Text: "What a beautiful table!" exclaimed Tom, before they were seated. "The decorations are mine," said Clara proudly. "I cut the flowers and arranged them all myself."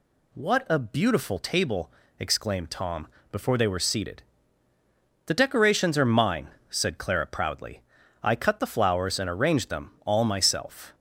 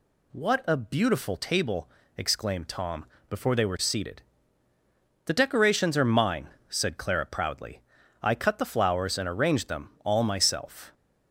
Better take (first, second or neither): neither